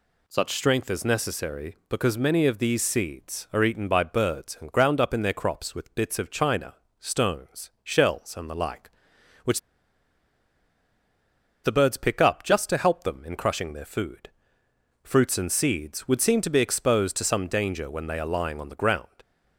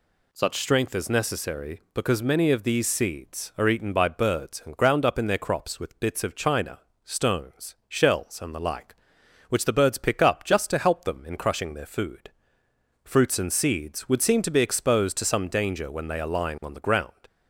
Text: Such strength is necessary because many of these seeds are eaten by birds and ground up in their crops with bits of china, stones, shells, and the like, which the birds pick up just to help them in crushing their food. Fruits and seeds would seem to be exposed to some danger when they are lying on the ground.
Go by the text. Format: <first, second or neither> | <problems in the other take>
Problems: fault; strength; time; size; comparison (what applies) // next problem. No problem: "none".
second | pauses between "which" and "the"; strong; at 9.5 s; 2.0 s long